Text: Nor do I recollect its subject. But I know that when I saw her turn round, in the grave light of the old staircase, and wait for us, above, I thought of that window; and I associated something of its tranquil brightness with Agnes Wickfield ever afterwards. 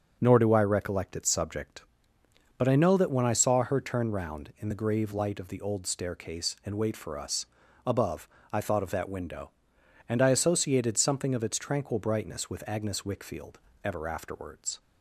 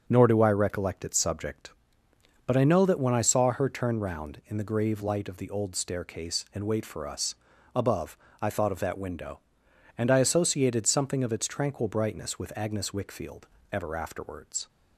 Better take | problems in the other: neither | starts louder than the rest; the same in both // pauses between "Wickfield" and "ever"; slight; the same in both

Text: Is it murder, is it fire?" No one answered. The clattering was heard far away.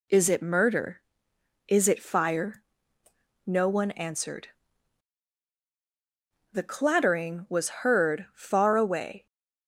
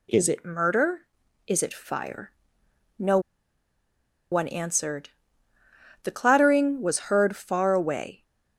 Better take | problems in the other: first | pauses between "No" and "one"; at 3.1 s; 1.1 s long

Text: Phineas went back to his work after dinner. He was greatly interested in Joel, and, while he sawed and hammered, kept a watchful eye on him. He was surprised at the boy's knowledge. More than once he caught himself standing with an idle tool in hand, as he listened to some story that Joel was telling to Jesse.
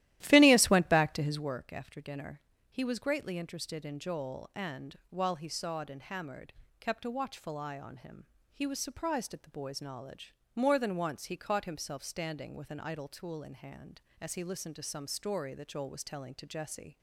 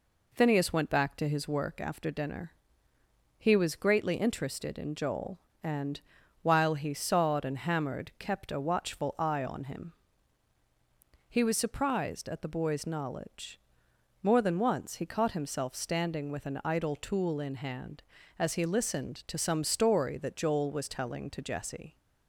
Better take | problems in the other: second | starts louder than the rest; strong; until 1.5 s; 14.5 dB

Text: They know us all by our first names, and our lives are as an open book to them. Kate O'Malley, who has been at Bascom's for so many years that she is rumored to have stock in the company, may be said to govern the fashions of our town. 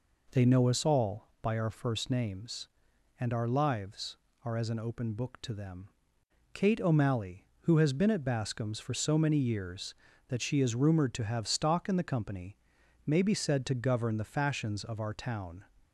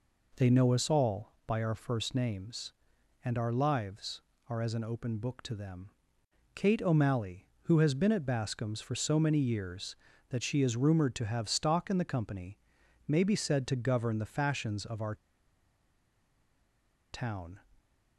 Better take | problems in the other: first | pauses between "our" and "town"; strong; at 15.1 s; 1.9 s long

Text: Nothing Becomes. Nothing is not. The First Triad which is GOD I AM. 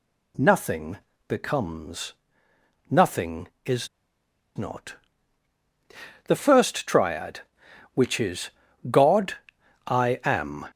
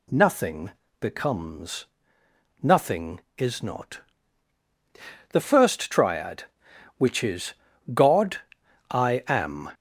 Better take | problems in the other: second | pauses between "Nothing" and "Becomes"; slight; at 0.9 s; 0.30 s long; slight in the second // pauses between "is" and "not"; noticeable; at 3.8 s; 0.68 s long // pauses between "is" and "GOD"; at 8.4 s; 0.40 s long; also in the second // pauses between "GOD" and "I"; noticeable; at 9.3 s; 0.50 s long; noticeable in the second

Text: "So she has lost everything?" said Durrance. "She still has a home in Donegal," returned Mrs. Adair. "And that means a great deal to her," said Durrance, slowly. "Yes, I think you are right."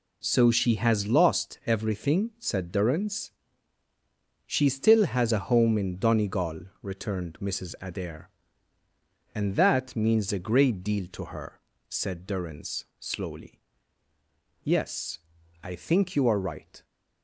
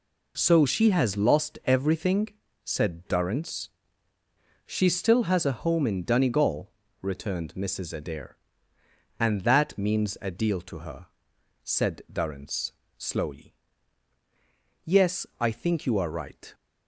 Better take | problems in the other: first | skips "great"; at 10.3 s

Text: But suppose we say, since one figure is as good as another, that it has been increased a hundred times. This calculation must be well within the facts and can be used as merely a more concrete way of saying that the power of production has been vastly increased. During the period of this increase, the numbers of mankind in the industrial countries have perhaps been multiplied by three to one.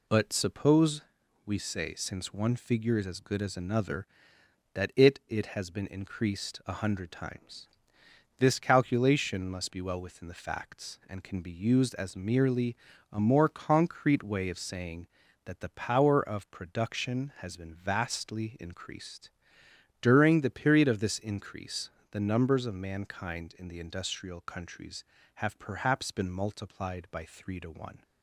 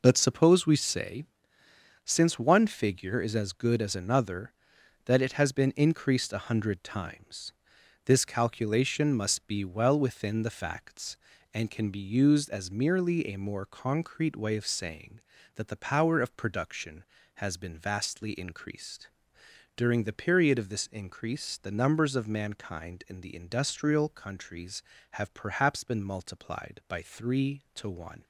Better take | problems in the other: second | pauses between "suppose" and "we"; noticeable; at 1.0 s; 0.46 s long // says "it" twice; at 5.2 s // pauses between "merely" and "a"; slight; at 12.7 s; 0.36 s long

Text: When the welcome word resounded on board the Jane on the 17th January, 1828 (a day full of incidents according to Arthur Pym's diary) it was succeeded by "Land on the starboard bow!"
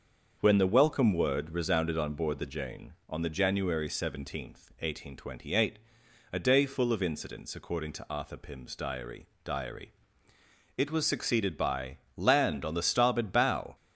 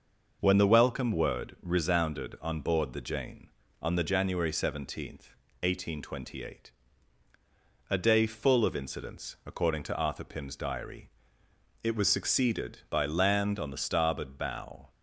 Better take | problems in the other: second | starts louder than the rest; until 1.4 s; 6.5 dB // says "diary" twice; at 9.4 s // pauses between "by" and "Land"; slight; at 11.9 s; 0.18 s long

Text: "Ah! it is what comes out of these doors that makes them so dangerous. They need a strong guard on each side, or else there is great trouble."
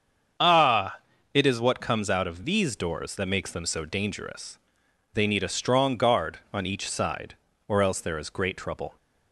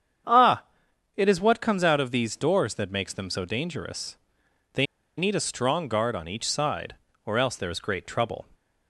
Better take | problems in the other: first | starts louder than the rest; strong; until 1.8 s; 8 dB; strong in the first // pauses between "They" and "need"; slight; at 4.8 s; 0.33 s long

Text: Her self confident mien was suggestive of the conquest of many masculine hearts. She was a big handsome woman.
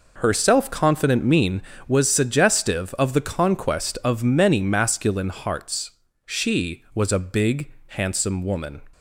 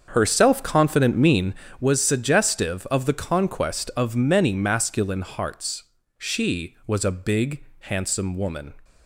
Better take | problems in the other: first | starts louder than the rest; until 1.7 s; 7 dB // pauses between "big" and "handsome"; slight; at 7.6 s; 0.18 s long; slight in the first

